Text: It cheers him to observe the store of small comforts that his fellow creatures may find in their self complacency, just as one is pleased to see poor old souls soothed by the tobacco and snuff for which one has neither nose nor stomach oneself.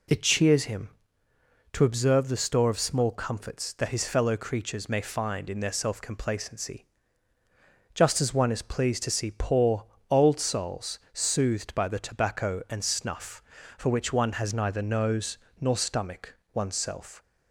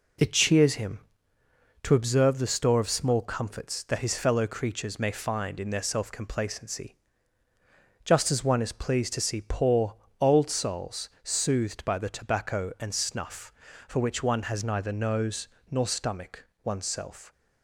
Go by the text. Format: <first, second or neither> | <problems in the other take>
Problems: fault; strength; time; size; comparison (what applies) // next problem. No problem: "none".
first | gets quieter; noticeable; throughout; 4.5 dB // pauses between "poor" and "old"; slight; at 9.9 s; 0.24 s long; slight in the first // pauses between "souls" and "soothed"; slight; at 11.0 s; 0.16 s long; slight in the first // pauses between "nose" and "nor"; slight; at 15.4 s; 0.24 s long; slight in the first // pauses between "stomach" and "oneself"; slight; at 16.4 s; 0.22 s long; slight in the first